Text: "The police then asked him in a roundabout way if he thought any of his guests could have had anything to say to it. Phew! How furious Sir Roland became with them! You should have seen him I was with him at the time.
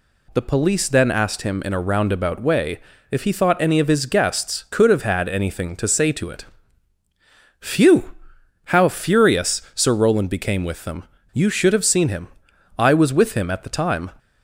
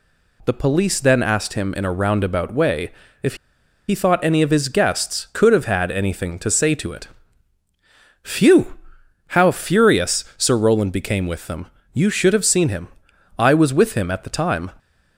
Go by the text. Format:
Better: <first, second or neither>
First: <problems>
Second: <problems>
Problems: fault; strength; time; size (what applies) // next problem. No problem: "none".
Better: first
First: pauses between "way" and "if"; slight; at 2.7 s; 0.30 s long // pauses between "him" and "I"; noticeable; at 12.2 s; 0.50 s long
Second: pauses between "way" and "if"; slight; at 2.9 s; 0.30 s long // pauses between "if" and "he"; noticeable; at 3.3 s; 0.53 s long // pauses between "him" and "I"; noticeable; at 12.8 s; 0.50 s long